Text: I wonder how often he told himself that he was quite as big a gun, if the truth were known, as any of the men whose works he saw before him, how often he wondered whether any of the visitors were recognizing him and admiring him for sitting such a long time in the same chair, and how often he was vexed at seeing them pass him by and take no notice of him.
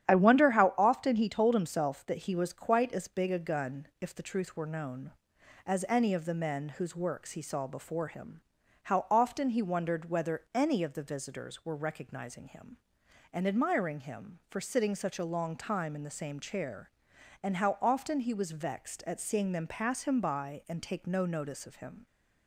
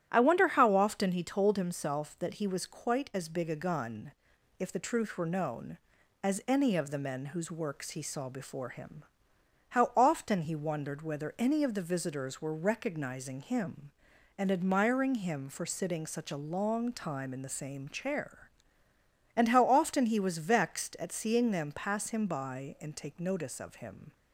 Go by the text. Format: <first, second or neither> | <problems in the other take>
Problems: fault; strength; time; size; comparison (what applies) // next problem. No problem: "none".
first | starts louder than the rest; strong; until 1.1 s; 10.5 dB; strong in the first // skips "no"; at 23.2 s